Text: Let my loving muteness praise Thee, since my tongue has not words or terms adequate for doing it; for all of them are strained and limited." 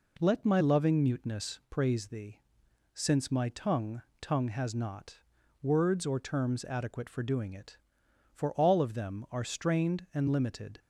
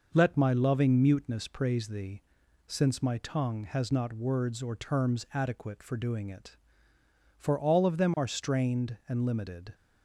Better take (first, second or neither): second